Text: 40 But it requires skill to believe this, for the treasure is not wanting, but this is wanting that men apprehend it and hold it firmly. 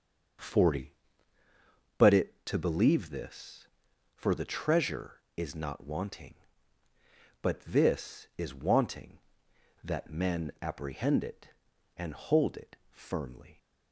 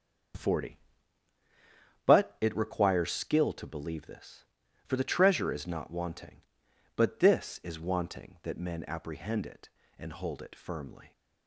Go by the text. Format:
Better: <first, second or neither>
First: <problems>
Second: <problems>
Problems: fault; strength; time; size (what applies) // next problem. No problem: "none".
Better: second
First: skips "requires skill"; at 2.4 s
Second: none